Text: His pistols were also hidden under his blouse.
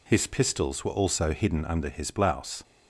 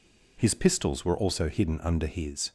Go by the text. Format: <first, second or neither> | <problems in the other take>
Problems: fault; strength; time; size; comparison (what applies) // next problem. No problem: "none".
first | stops before "blouse"; at 2.4 s